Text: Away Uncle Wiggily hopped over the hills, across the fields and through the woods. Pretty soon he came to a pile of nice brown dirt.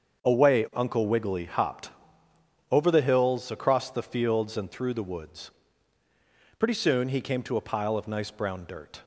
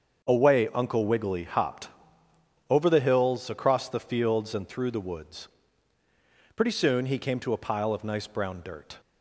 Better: neither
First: starts louder than the rest; until 1.2 s; 7 dB // pauses between "hopped" and "over"; noticeable; at 1.8 s; 0.82 s long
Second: starts louder than the rest; until 1.2 s; 6.5 dB // pauses between "hopped" and "over"; noticeable; at 1.8 s; 0.82 s long

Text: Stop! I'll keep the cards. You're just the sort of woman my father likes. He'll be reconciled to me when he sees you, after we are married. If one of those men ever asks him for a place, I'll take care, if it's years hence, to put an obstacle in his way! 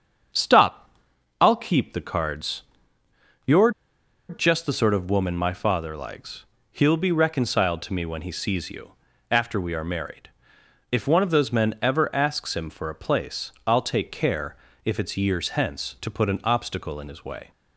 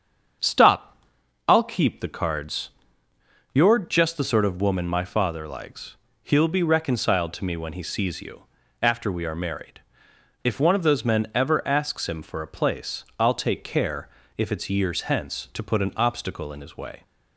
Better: second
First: starts louder than the rest; strong; until 1.8 s; 7 dB // pauses between "You're" and "just"; noticeable; at 3.7 s; 0.58 s long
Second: starts louder than the rest; strong; until 1.9 s; 7.5 dB

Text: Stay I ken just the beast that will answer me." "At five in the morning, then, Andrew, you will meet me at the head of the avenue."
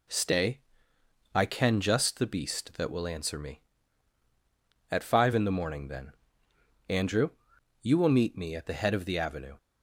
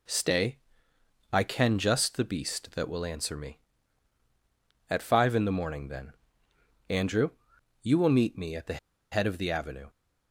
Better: first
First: pauses between "Stay" and "I"; noticeable; at 0.6 s; 0.74 s long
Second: pauses between "Stay" and "I"; noticeable; at 0.5 s; 0.74 s long // pauses between "the" and "head"; slight; at 8.7 s; 0.33 s long

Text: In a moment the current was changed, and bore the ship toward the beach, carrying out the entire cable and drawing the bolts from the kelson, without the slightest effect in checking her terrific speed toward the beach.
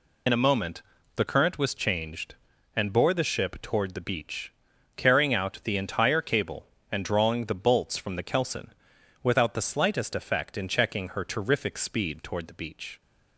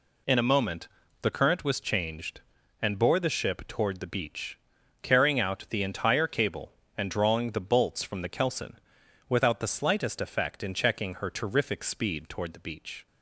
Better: second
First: loses the start of "In"; at 0.2 s; 60 ms // pauses between "moment" and "the"; slight; at 0.8 s; 0.36 s long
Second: pauses between "moment" and "the"; slight; at 0.8 s; 0.36 s long

